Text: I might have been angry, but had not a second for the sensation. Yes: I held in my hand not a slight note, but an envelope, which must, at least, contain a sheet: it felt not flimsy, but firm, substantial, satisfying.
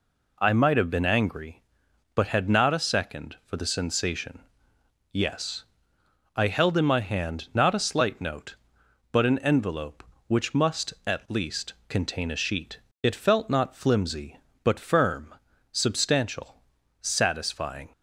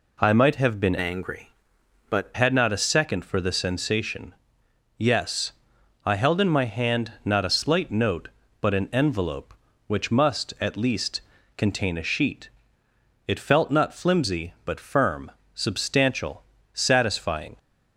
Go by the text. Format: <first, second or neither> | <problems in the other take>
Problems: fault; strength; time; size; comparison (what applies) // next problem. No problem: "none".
first | changes voice from "angry" to "but"; from 1.0 to 2.3 s; 1.3 s long